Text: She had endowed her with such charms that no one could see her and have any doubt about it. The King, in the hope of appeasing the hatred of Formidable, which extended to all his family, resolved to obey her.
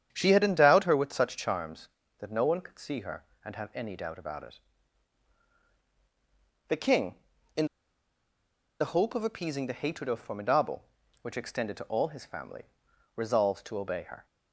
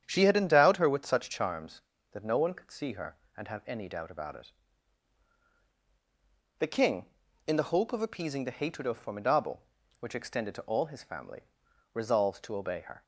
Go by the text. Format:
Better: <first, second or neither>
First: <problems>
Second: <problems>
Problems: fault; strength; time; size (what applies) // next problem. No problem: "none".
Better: second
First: starts louder than the rest; strong; until 1.1 s; 9 dB // pauses between "in" and "the"; at 7.6 s; 1.1 s long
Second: starts louder than the rest; strong; until 1.0 s; 9 dB